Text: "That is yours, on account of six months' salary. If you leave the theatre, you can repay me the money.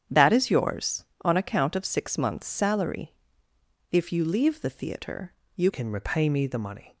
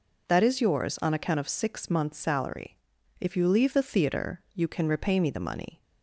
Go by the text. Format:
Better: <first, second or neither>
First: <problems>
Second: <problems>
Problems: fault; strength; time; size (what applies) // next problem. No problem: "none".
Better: second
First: starts louder than the rest; strong; until 1.2 s; 9 dB // changes voice at "can"; from 5.7 s on; 1.2 s long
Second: none